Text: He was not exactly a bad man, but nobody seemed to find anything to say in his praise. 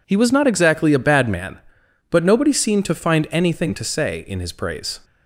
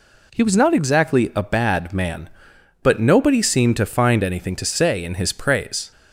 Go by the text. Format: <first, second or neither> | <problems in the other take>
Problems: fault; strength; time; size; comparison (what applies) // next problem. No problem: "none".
neither | none